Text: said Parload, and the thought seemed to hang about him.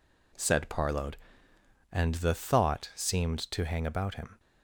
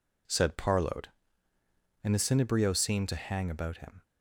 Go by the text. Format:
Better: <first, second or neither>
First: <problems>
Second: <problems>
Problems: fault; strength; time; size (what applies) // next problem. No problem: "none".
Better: first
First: none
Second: says "cinebrio" for "thought"; at 2.1 s